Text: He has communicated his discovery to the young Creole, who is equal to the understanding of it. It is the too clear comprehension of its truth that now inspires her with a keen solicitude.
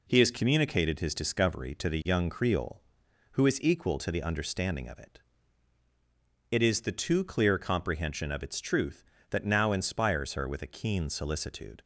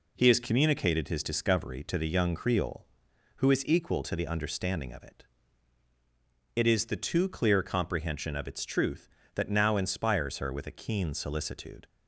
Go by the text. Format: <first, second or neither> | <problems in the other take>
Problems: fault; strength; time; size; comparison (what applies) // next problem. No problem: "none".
neither | none